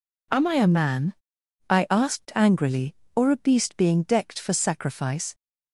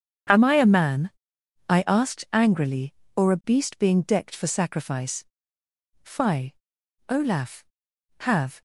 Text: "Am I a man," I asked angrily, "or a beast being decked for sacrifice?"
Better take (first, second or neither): first